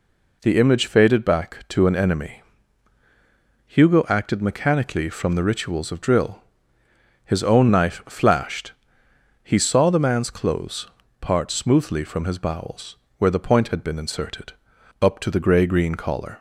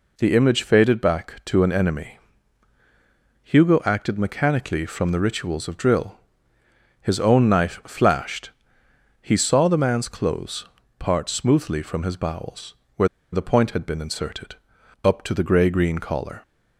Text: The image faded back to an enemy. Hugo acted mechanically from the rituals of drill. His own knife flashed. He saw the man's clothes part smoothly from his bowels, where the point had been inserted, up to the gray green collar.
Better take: first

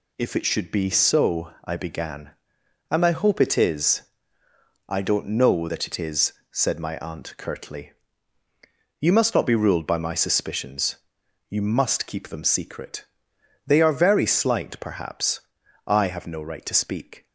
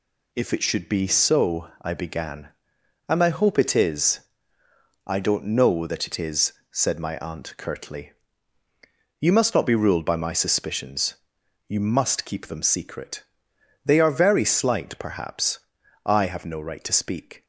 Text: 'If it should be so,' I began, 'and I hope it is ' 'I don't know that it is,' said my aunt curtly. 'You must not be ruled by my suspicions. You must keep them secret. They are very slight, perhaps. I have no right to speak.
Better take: neither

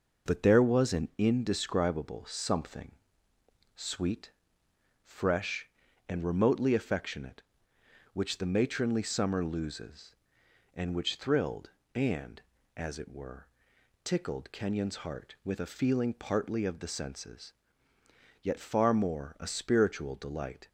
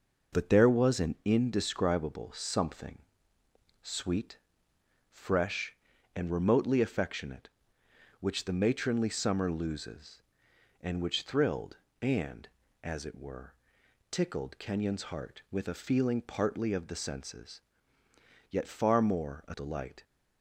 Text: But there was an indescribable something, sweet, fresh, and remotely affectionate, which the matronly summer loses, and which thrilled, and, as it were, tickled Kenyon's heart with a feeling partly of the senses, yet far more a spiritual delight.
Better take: first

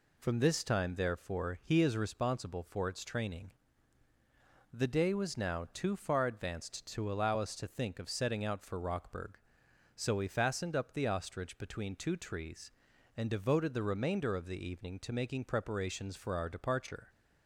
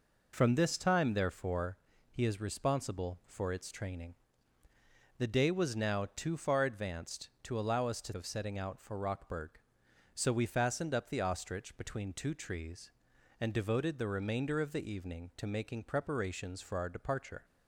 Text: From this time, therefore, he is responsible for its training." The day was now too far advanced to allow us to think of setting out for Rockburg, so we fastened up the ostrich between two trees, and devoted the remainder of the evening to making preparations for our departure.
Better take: first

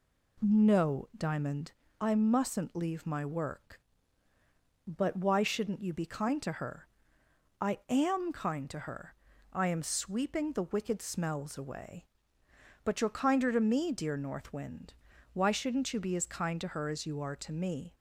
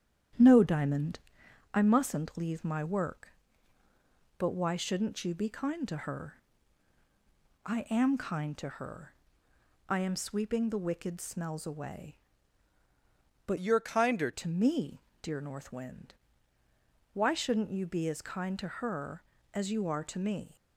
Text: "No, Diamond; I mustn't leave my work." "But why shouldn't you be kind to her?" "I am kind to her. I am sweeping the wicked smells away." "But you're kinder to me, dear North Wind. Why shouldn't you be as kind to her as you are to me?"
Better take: first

